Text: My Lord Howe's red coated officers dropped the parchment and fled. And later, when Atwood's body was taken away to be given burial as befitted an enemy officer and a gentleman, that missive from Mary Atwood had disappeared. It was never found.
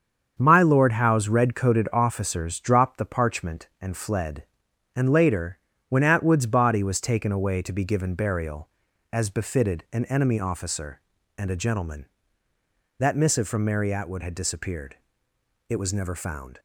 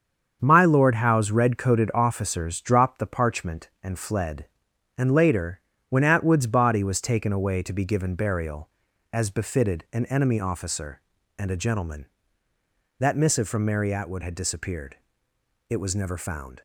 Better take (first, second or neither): neither